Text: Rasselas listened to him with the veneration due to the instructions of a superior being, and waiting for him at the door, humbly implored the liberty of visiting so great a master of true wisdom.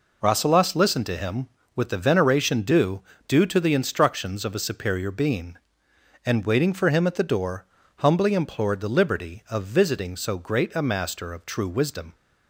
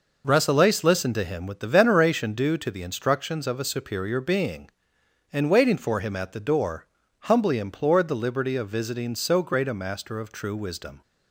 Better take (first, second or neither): second